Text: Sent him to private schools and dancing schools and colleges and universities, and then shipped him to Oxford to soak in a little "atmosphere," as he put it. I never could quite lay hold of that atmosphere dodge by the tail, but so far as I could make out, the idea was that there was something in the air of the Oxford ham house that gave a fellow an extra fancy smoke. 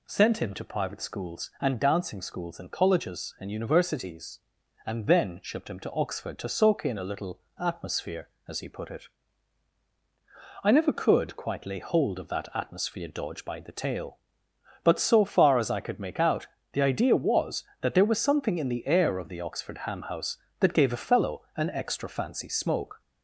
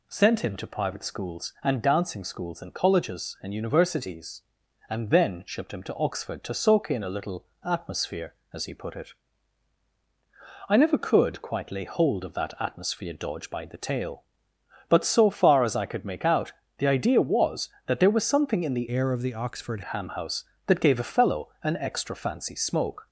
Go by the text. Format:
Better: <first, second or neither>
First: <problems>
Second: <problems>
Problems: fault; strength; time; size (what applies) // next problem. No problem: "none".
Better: first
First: pauses between "little" and "atmosphere"; slight; at 7.3 s; 0.20 s long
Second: pauses between "little" and "atmosphere"; slight; at 7.4 s; 0.20 s long // changes voice from "air" to "Oxford"; from 18.8 to 19.8 s; 1.0 s long